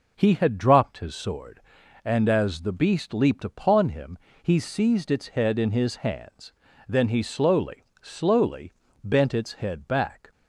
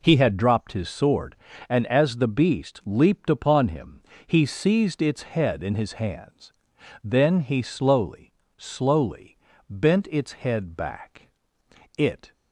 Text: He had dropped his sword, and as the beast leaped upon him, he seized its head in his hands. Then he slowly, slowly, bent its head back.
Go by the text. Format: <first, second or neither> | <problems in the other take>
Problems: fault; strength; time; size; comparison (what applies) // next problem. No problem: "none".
first | goes on to say "It"; slight; from 11.9 s on; 0.36 s long